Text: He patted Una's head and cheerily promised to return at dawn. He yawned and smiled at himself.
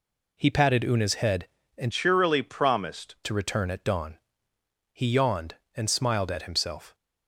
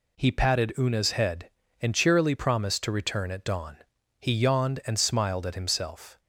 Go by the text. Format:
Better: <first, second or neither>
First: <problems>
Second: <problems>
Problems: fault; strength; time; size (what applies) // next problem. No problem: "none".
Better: second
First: changes voice from "cheerily" to "promised"; from 1.9 to 3.1 s; 1.2 s long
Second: none